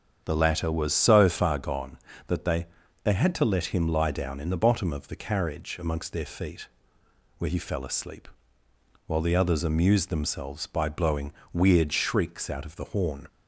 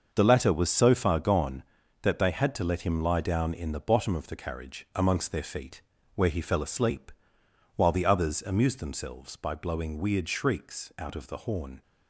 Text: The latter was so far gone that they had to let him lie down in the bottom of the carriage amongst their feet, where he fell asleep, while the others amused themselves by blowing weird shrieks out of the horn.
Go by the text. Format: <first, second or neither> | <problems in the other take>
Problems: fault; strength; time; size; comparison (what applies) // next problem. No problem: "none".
second | starts louder than the rest; strong; until 1.2 s; 7.5 dB; also in the second // says "they" twice; at 3.0 s // pauses between "blowing" and "weird"; slight; at 11.3 s; 0.20 s long